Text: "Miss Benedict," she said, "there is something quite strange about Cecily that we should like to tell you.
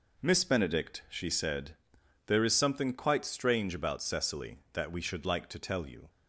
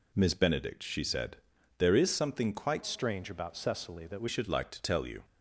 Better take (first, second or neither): first